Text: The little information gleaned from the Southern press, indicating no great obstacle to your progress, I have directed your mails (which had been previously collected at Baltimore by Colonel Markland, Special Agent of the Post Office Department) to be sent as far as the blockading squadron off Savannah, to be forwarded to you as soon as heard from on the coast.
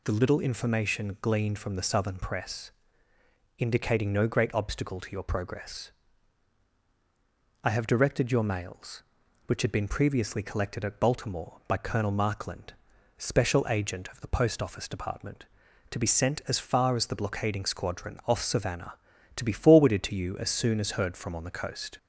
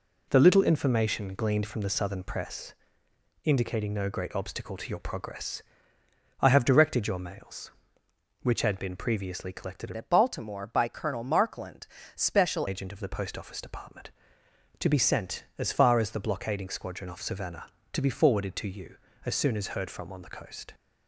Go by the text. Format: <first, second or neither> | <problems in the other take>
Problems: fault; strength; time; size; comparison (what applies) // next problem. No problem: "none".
first | changes voice from "at" to "Special"; from 9.9 to 12.6 s; 2.7 s long